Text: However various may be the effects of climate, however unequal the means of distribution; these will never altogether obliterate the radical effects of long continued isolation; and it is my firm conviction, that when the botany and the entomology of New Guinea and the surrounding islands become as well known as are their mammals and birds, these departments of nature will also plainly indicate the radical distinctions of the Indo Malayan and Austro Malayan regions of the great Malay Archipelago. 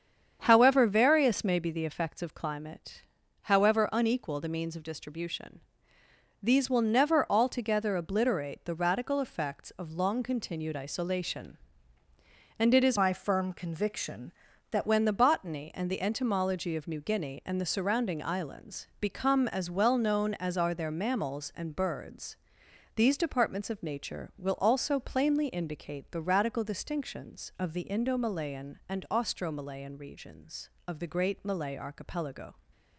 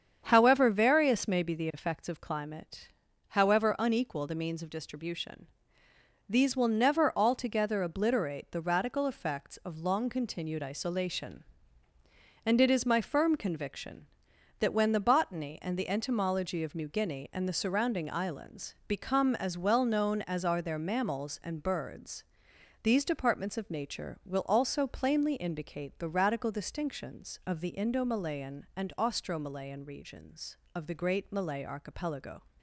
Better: second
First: starts louder than the rest; strong; until 1.4 s; 8 dB // changes voice from "my" to "that"; from 12.9 to 14.8 s; 1.9 s long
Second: starts louder than the rest; strong; until 1.2 s; 8 dB

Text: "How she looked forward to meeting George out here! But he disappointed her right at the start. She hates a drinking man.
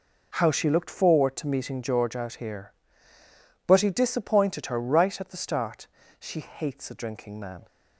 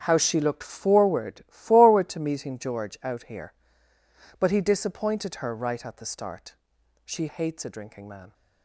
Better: first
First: none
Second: starts louder than the rest; strong; until 1.0 s; 8.5 dB // says "forward" twice; at 1.4 s

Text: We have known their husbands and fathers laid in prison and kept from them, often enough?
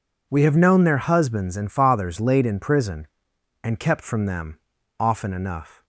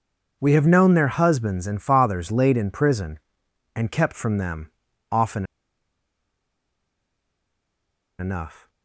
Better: first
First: none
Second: pauses between "often" and "enough"; strong; at 5.4 s; 2.7 s long

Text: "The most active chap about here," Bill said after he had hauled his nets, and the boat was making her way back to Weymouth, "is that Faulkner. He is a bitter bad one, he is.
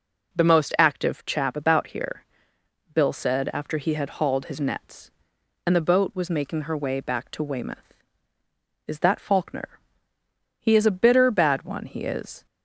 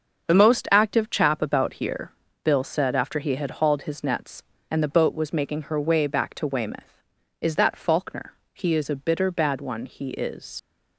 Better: first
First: none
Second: starts louder than the rest; until 1.3 s; 6.5 dB // leaves "is" unfinished; at 10.5 s; 65 ms

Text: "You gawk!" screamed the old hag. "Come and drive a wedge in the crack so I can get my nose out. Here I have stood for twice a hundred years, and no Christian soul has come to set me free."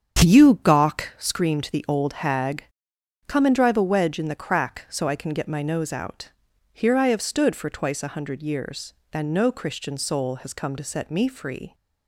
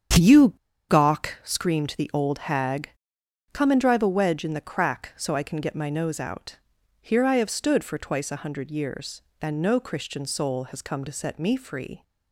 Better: first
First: starts louder than the rest; strong; until 1.4 s; 8 dB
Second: starts louder than the rest; strong; until 1.6 s; 8 dB // pauses between "You" and "gawk"; at 0.4 s; 0.39 s long

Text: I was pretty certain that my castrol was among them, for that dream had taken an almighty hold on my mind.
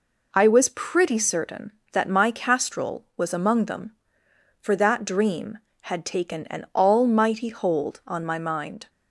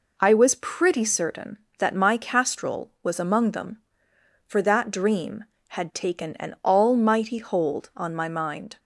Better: neither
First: none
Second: none

